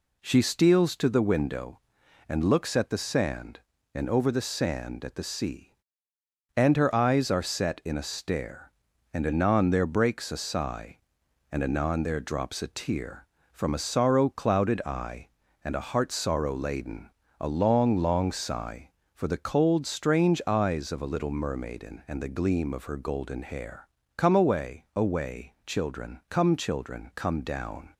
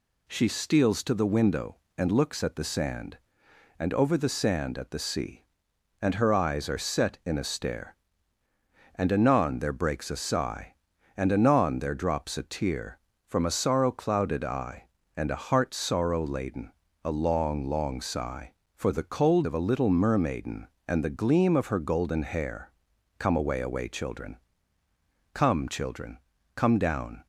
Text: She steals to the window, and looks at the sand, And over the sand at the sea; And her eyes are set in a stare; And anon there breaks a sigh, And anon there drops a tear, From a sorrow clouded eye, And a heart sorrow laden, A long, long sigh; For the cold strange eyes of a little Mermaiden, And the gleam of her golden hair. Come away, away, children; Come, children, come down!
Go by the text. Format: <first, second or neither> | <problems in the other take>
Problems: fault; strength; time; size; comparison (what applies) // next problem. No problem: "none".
first | skips "strange eyes"; at 19.4 s